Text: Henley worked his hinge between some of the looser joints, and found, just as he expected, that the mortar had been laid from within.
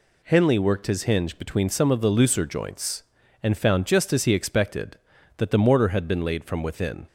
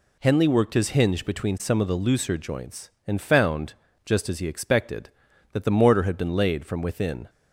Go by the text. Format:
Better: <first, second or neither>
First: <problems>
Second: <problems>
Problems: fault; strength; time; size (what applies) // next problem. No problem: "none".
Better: neither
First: none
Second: none